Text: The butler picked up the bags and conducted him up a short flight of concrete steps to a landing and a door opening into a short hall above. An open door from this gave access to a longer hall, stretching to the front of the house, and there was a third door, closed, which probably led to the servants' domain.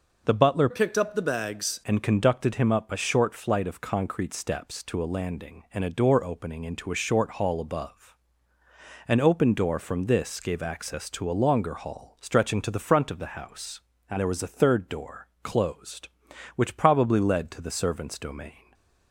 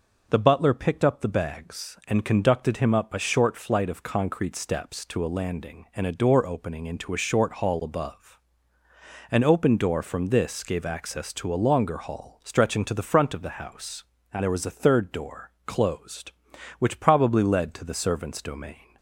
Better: second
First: changes voice from "picked" to "bags"; from 0.7 to 1.8 s; 1.1 s long // stays silent after the last word; slight; from 18.5 s on; 0.6 s long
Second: none

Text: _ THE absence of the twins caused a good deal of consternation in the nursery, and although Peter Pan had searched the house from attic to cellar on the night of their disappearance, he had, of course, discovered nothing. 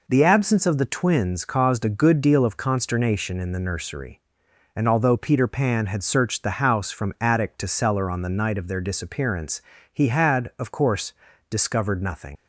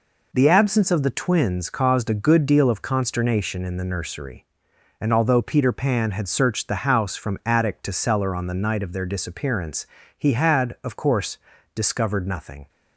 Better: second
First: leaves "nothing" unfinished; at 12.3 s; 80 ms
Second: none

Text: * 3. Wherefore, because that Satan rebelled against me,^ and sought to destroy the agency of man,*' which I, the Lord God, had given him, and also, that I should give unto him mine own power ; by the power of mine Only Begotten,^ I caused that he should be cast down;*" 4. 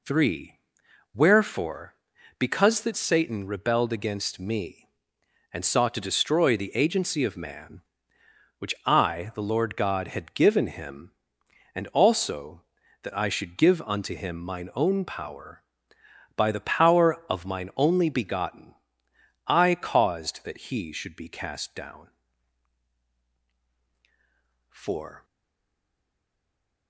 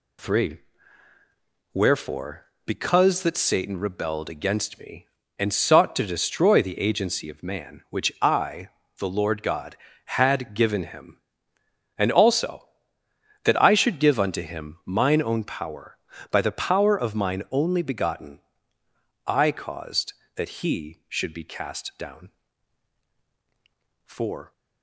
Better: second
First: stays silent after the last word; noticeable; from 25.2 s on; 1.6 s long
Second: none

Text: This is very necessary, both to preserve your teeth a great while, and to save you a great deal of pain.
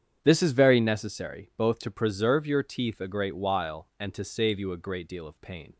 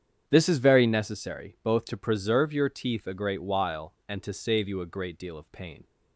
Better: neither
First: starts louder than the rest; strong; until 1.2 s; 8.5 dB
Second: starts louder than the rest; strong; until 1.2 s; 8.5 dB

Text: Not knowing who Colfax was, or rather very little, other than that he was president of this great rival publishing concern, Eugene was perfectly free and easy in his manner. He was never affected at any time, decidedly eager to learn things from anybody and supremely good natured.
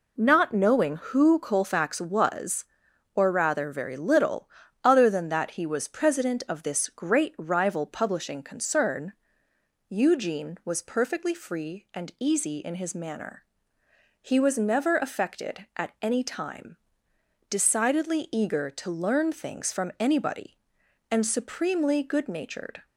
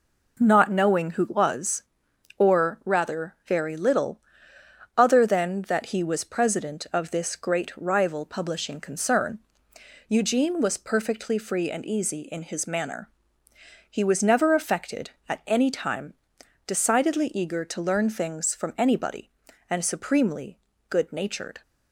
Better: first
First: none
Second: skips "Colfax"; at 1.2 s // pauses between "supremely" and "good"; slight; at 20.5 s; 0.30 s long

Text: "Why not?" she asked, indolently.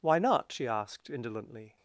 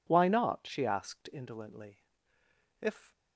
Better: first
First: none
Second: goes on to say "If"; slight; from 2.7 s on; 0.32 s long

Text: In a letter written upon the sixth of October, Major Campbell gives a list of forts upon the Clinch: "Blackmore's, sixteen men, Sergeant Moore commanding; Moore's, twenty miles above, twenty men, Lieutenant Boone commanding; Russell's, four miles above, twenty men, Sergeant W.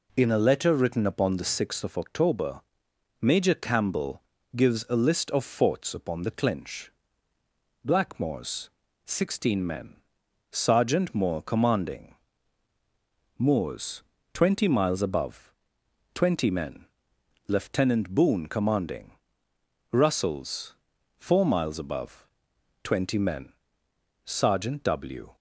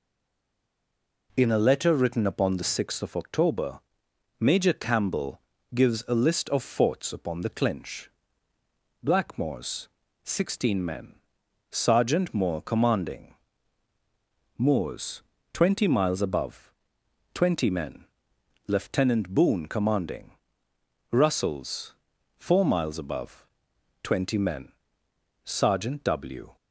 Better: first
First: pauses between "Campbell" and "gives"; slight; at 4.2 s; 0.34 s long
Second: stays silent before the first word; noticeable; until 1.2 s; 1.2 s long // pauses between "Campbell" and "gives"; slight; at 5.3 s; 0.34 s long

